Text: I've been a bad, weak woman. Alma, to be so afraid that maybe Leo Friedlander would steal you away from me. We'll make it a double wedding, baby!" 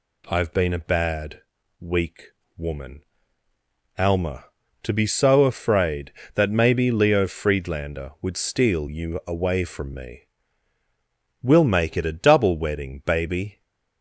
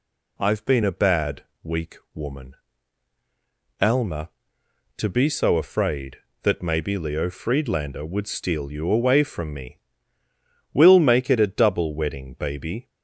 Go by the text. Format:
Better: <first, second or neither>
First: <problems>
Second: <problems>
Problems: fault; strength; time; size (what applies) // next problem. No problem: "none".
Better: neither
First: pauses between "weak" and "woman"; slight; at 2.2 s; 0.28 s long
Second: pauses between "weak" and "woman"; slight; at 1.9 s; 0.18 s long